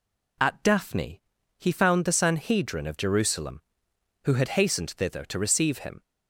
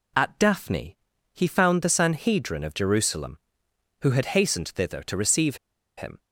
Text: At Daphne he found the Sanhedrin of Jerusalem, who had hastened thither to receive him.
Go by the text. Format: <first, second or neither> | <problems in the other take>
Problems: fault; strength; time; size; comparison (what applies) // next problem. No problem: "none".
first | pauses between "Daphne" and "he"; at 0.9 s; 0.40 s long; also in the first // pauses between "receive" and "him"; at 5.5 s; 0.39 s long